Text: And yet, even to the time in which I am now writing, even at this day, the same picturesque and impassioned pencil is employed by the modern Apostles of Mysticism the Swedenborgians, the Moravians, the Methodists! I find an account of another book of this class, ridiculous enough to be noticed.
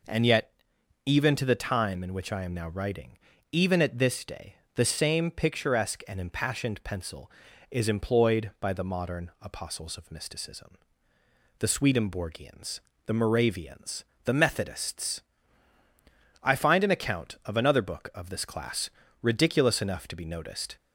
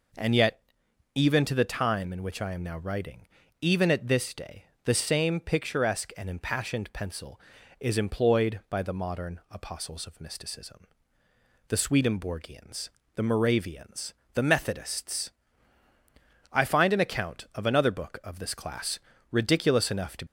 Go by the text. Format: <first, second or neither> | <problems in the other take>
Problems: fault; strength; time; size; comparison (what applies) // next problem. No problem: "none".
first | pauses between "Mysticism" and "the"; noticeable; at 10.8 s; 0.88 s long; noticeable in the first // stops before "be noticed"; at 20.2 s